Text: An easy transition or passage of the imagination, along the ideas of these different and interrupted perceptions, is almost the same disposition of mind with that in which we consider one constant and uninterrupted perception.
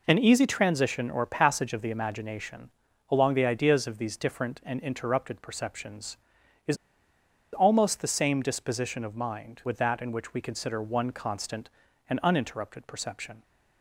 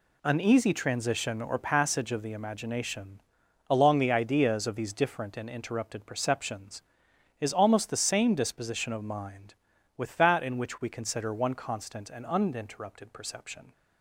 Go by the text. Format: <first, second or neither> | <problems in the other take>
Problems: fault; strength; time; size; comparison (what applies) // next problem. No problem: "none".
second | pauses between "is" and "almost"; noticeable; at 6.7 s; 0.77 s long